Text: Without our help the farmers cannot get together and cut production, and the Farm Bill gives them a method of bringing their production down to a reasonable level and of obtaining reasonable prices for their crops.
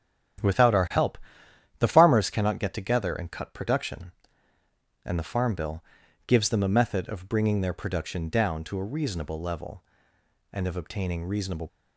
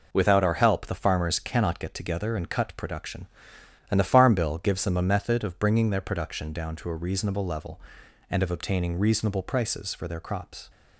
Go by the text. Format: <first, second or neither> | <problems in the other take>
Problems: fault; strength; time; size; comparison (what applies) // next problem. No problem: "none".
second | starts louder than the rest; strong; until 2.0 s; 10.5 dB // pauses between "help" and "the"; noticeable; at 1.1 s; 0.62 s long // pauses between "Bill" and "gives"; at 5.8 s; 0.44 s long // stops before "prices for their crops"; at 11.6 s